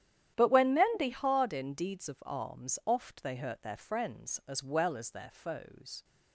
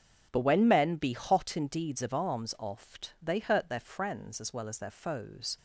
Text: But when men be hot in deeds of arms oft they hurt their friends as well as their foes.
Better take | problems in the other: second | starts louder than the rest; strong; until 1.3 s; 10.5 dB; also in the second // says "hard" for "hot"; at 1.0 s

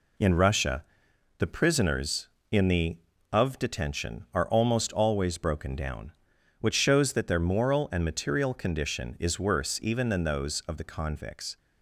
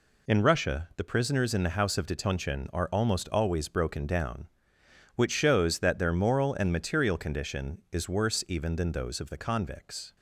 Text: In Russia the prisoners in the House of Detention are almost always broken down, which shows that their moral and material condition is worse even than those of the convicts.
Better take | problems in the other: second | pauses between "Russia" and "the"; noticeable; at 0.8 s; 0.54 s long // skips "House"; at 3.1 s

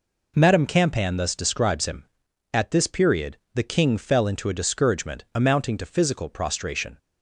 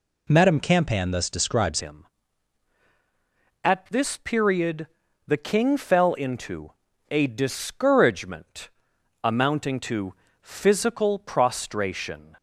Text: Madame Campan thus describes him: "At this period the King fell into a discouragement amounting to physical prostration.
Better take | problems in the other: first | changes voice at "him"; from 1.8 s on; 10.5 s long // pauses between "period" and "the"; at 4.8 s; 0.38 s long; slight in the first // pauses between "into" and "a"; at 6.7 s; 0.38 s long // pauses between "discouragement" and "amounting"; noticeable; at 8.6 s; 0.56 s long // pauses between "to" and "physical"; slight; at 10.1 s; 0.28 s long

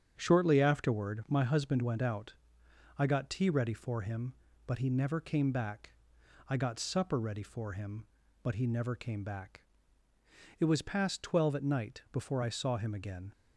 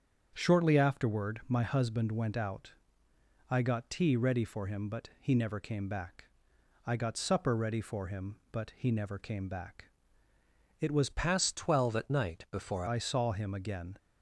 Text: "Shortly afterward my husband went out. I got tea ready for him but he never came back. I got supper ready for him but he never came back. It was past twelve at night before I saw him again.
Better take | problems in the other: first | starts louder than the rest; strong; until 1.3 s; 7 dB; strong in the first // changes voice from "past" to "before"; from 11.0 to 12.8 s; 1.8 s long

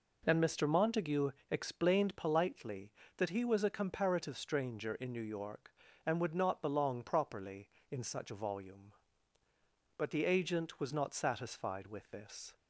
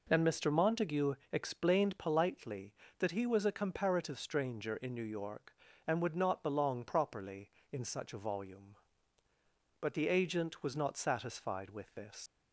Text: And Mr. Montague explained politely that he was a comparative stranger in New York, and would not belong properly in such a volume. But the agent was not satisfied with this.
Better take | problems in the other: first | pauses between "Montague" and "explained"; slight; at 1.1 s; 0.18 s long; slight in the first // leaves "this" unfinished; at 12.2 s; 130 ms

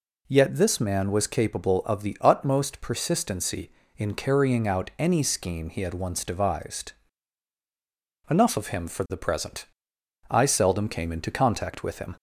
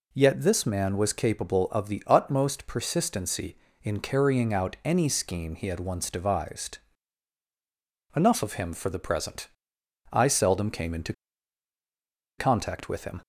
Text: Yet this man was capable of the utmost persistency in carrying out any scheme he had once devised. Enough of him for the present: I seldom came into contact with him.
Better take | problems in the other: first | pauses between "into" and "contact"; strong; at 11.1 s; 1.2 s long

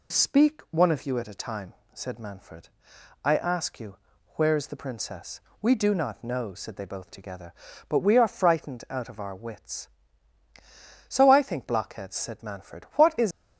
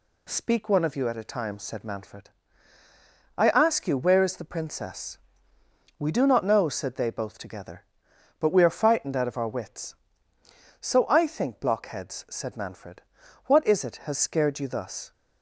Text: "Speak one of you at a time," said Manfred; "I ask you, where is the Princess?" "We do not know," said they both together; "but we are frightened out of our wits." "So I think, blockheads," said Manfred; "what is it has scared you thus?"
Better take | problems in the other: second | stops before "it has scared you thus"; at 13.3 s

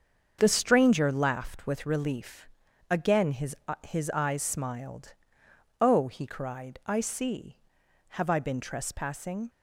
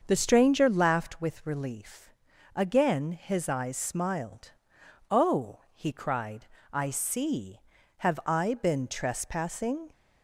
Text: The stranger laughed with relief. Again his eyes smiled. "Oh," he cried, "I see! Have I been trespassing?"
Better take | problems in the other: second | starts louder than the rest; until 1.4 s; 7 dB; also in the second // says "his" twice; at 3.8 s

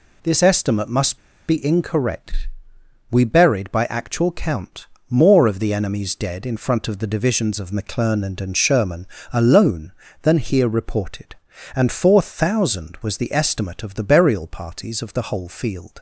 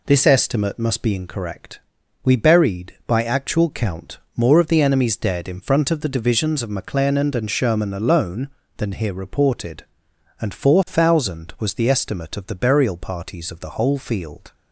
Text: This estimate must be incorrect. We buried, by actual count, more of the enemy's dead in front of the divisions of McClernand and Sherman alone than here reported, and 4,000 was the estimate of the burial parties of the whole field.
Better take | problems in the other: second | pauses between "must" and "be"; slight; at 1.1 s; 0.28 s long // pauses between "Sherman" and "alone"; slight; at 9.0 s; 0.26 s long

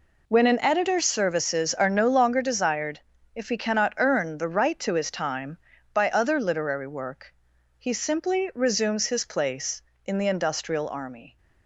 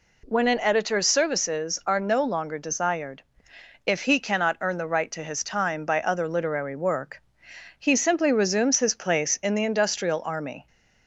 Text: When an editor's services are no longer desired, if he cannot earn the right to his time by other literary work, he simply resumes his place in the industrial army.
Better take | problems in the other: second | gets quieter; strong; throughout; 11.5 dB

